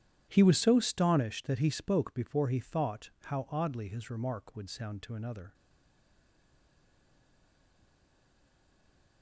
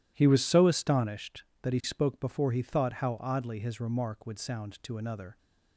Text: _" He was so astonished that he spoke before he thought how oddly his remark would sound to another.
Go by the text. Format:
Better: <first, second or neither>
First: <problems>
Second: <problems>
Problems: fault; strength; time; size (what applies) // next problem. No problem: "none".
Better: second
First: starts louder than the rest; strong; until 1.3 s; 11.5 dB // stays silent after the last word; strong; from 5.5 s on; 3.7 s long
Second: none